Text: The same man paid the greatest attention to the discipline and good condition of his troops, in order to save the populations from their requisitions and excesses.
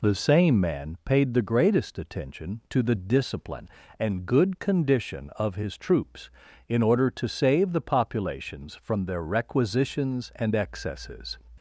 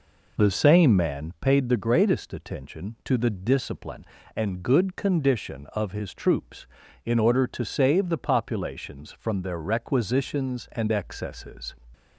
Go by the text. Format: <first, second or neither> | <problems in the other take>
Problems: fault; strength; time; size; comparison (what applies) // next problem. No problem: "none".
first | starts louder than the rest; noticeable; until 1.6 s; 4.5 dB